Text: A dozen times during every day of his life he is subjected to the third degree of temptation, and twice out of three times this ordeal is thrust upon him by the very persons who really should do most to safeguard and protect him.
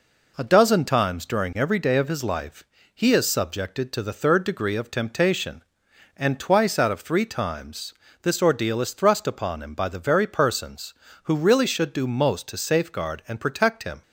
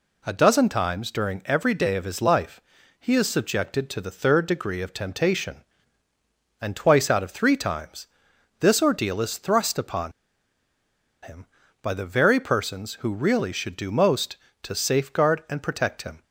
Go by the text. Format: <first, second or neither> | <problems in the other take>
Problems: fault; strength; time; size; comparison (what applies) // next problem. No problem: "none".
first | pauses between "life" and "he"; at 2.6 s; 0.40 s long; slight in the first // pauses between "times" and "this"; noticeable; at 8.0 s; 0.54 s long; slight in the first // pauses between "upon" and "him"; at 10.1 s; 1.1 s long